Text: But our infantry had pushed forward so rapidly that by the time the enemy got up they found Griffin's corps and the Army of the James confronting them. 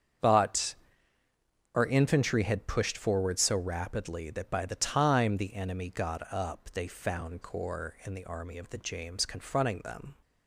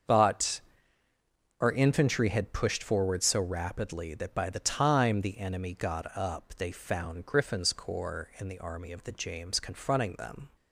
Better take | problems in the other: second | starts louder than the rest; strong; until 2.2 s; 8 dB; also in the second // pauses between "But" and "our"; at 0.7 s; 1.0 s long; also in the second // skips "Griffin's"; at 7.4 s

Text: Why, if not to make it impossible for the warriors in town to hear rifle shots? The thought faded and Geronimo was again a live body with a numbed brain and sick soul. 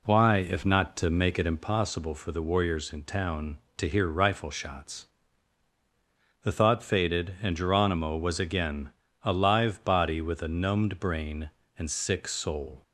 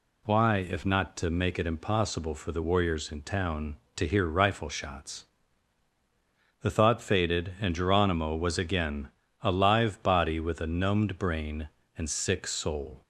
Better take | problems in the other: second | starts louder than the rest; slight; until 1.7 s; 3 dB // pauses between "again" and "a"; slight; at 8.8 s; 0.34 s long; slight in the second

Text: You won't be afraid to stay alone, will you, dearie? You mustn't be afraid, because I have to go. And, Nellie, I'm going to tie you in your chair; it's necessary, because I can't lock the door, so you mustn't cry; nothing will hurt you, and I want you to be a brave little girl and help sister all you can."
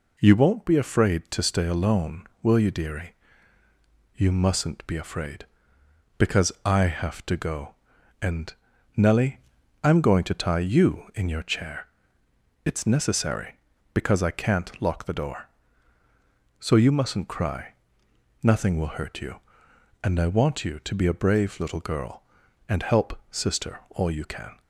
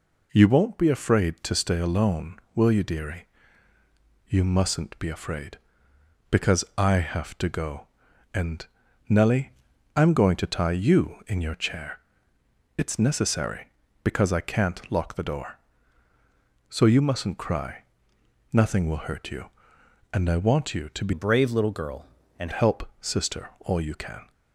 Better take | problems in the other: first | changes voice from "a" to "and"; from 21.1 to 22.5 s; 1.4 s long

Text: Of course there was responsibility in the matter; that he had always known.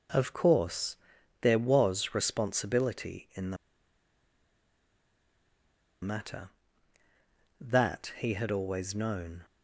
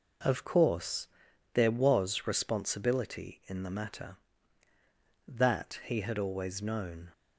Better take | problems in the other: second | pauses between "course" and "there"; at 0.9 s; 0.44 s long; also in the second // pauses between "the" and "matter"; strong; at 3.5 s; 2.4 s long

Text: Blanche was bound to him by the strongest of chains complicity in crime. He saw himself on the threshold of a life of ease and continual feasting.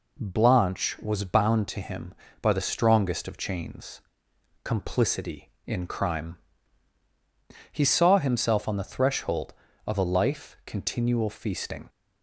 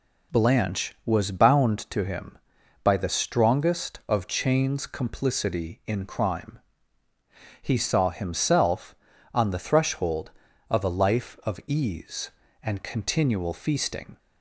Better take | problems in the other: second | pauses between "chains" and "complicity"; noticeable; at 3.9 s; 0.64 s long // skips "of ease and"; at 10.6 s

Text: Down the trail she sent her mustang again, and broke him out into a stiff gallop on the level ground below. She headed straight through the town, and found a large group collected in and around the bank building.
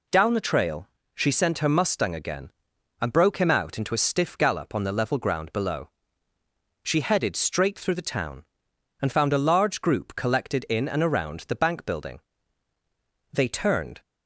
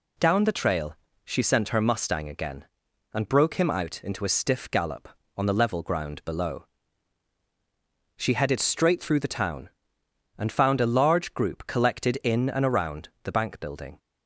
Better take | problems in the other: second | pauses between "trail" and "she"; slight; at 0.8 s; 0.26 s long; slight in the second // goes on to say "They turned"; noticeable; from 13.3 s on; 0.68 s long

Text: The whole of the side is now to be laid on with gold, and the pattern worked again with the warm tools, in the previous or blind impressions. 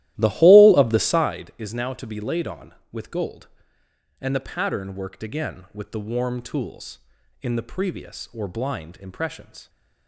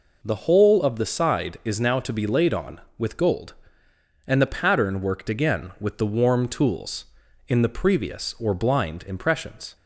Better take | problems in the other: second | starts louder than the rest; strong; until 1.3 s; 14.5 dB

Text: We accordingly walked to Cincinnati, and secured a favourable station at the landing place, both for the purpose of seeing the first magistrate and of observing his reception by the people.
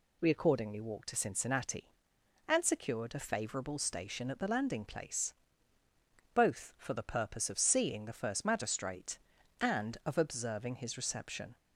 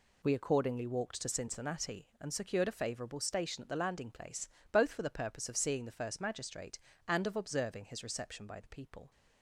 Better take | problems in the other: second | stops before "by the people"; at 11.5 s

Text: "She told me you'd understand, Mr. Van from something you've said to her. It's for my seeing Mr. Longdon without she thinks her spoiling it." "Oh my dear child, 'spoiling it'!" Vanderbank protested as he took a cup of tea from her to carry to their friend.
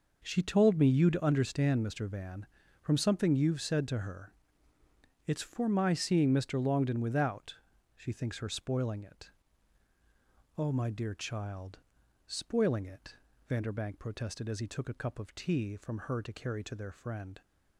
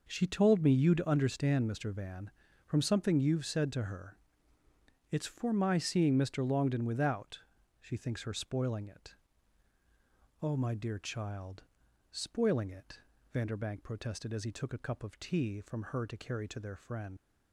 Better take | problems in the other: first | pauses between "without" and "she"; at 7.3 s; 0.42 s long; also in the first // leaves "friend" unfinished; at 17.1 s; 85 ms

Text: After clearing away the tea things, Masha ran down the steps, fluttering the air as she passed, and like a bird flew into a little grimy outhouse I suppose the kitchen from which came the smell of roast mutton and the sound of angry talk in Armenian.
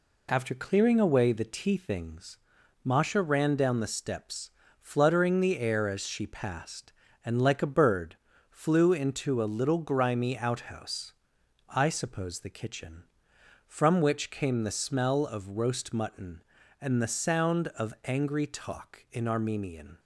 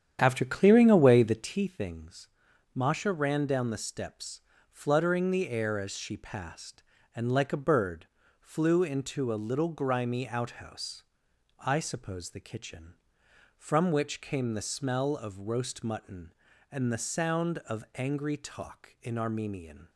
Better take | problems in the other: first | starts louder than the rest; strong; until 1.6 s; 9.5 dB // pauses between "bird" and "flew"; slight; at 8.0 s; 0.32 s long; slight in the first // pauses between "outhouse" and "I"; noticeable; at 11.0 s; 0.58 s long; noticeable in the first

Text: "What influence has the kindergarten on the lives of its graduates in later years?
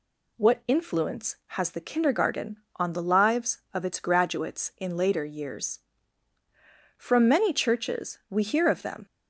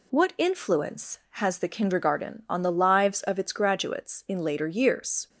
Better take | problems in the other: second | goes on to say "From many churches we hear of them"; strong; from 6.9 s on; 2.0 s long

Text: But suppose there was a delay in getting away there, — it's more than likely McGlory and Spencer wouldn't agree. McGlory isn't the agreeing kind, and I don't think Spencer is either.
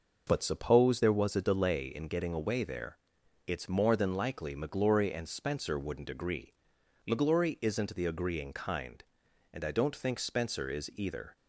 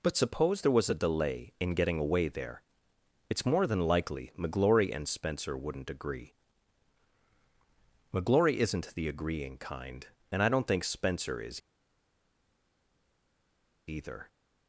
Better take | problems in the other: first | pauses between "is" and "either"; strong; at 11.6 s; 2.2 s long

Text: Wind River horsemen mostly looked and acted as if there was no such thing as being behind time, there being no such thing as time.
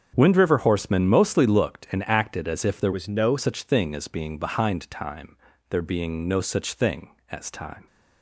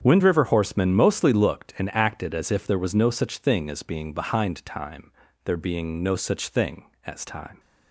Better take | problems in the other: second | starts louder than the rest; strong; until 1.1 s; 7.5 dB; strong in the second // changes voice from "was" to "no"; from 2.9 to 3.3 s; 0.4 s long

